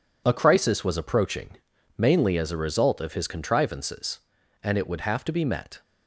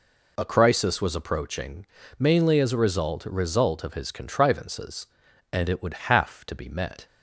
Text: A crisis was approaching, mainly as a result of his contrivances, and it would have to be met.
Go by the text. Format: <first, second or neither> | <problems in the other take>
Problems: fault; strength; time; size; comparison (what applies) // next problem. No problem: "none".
first | says "result" twice; at 3.2 s